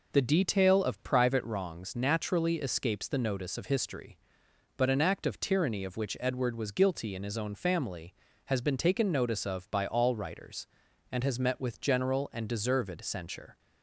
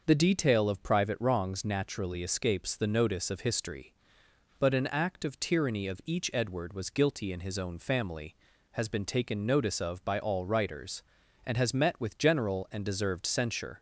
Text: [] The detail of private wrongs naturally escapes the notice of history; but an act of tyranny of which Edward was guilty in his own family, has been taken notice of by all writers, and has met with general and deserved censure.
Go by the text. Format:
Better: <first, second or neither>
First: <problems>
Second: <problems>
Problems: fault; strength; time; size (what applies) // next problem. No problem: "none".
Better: first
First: none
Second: starts louder than the rest; noticeable; until 1.0 s; 6 dB // says "each" for "which"; at 6.0 s